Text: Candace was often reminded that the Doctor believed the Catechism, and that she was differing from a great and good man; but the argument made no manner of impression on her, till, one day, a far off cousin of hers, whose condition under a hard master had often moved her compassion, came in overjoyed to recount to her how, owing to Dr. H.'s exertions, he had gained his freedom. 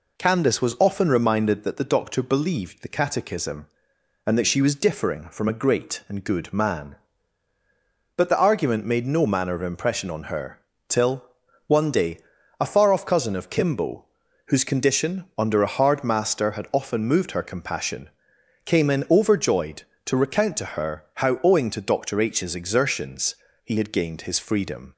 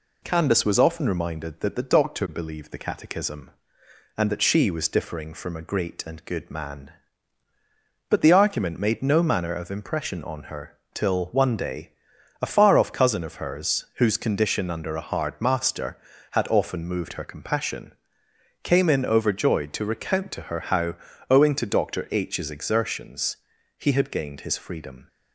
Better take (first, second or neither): second